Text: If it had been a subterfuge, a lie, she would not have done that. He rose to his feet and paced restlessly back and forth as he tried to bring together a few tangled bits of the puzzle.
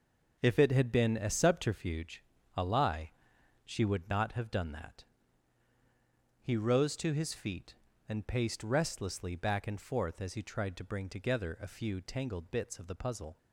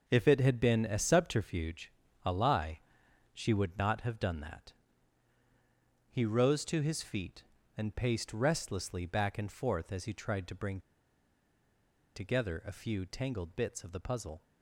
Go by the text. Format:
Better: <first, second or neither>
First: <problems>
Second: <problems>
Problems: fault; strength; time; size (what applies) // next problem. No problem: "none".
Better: first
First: none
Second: pauses between "bring" and "together"; strong; at 10.7 s; 1.3 s long